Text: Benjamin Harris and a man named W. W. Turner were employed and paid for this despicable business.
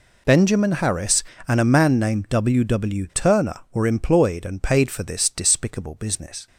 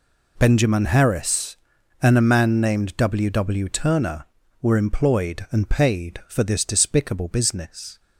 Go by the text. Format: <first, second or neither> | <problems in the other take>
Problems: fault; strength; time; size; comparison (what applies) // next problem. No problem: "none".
neither | none